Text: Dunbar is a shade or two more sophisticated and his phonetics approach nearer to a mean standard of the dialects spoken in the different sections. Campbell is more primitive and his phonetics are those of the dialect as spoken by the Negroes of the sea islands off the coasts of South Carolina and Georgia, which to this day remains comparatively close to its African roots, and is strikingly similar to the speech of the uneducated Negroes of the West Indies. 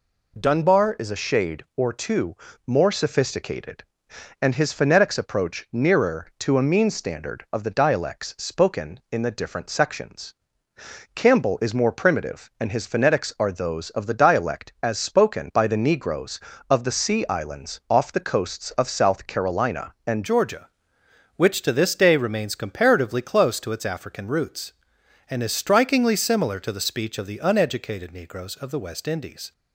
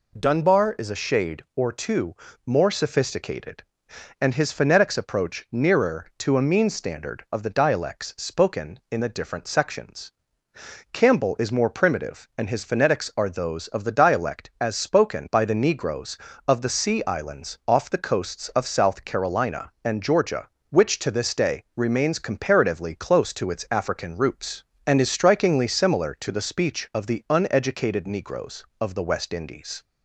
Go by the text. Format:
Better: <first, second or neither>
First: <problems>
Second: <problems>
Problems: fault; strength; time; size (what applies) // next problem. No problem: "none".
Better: second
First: pauses between "two" and "more"; slight; at 2.3 s; 0.30 s long // changes voice at "Georgia"; from 20.2 s on; 9.3 s long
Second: pauses between "two" and "more"; slight; at 2.1 s; 0.30 s long